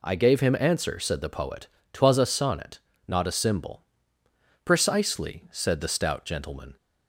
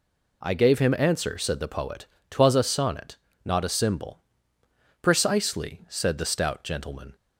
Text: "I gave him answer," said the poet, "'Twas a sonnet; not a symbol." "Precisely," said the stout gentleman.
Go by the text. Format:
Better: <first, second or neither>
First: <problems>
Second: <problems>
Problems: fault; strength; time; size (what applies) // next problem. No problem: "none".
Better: neither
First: none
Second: none